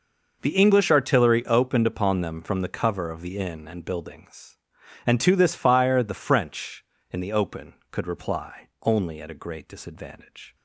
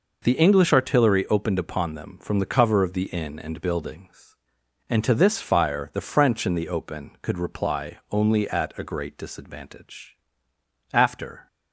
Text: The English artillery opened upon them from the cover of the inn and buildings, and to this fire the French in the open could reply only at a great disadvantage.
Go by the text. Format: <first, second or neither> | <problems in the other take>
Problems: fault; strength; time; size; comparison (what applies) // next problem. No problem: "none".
first | goes on to say "After"; from 10.9 s on; 0.54 s long